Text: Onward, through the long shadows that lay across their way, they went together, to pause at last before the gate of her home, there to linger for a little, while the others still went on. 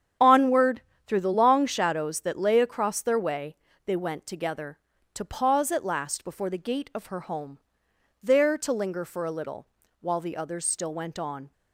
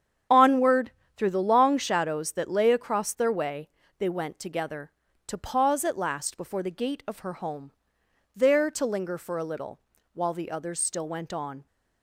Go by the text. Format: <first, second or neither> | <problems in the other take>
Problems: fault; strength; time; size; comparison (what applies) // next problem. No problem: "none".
neither | starts louder than the rest; strong; the same in both